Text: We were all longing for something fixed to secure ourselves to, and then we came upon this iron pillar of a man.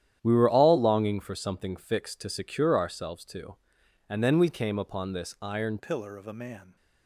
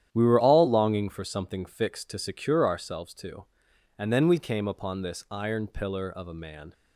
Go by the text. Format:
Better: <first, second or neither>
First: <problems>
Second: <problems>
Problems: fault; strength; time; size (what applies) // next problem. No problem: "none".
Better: second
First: starts louder than the rest; strong; until 1.2 s; 10.5 dB // changes voice at "pillar"; from 5.7 s on; 1.0 s long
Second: starts louder than the rest; strong; until 1.1 s; 10.5 dB